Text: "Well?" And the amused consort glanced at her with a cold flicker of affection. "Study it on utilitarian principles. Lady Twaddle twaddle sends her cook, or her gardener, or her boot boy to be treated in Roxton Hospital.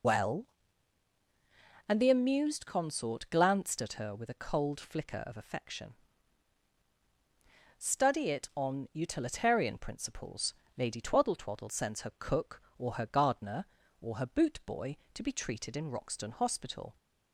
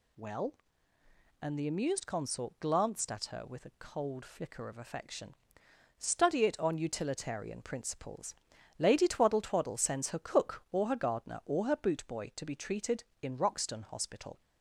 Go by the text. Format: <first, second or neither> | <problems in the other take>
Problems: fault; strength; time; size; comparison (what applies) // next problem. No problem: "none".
second | loses the start of "Well"; at 0.0 s; 85 ms